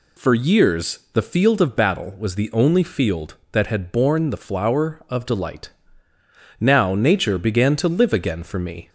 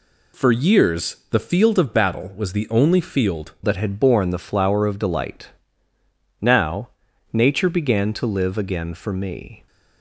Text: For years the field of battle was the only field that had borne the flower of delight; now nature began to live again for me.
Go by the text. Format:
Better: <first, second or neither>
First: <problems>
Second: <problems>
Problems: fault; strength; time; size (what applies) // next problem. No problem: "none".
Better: first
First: none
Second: changes voice at "that"; from 3.6 s on; 6.0 s long // pauses between "now" and "nature"; noticeable; at 6.8 s; 0.46 s long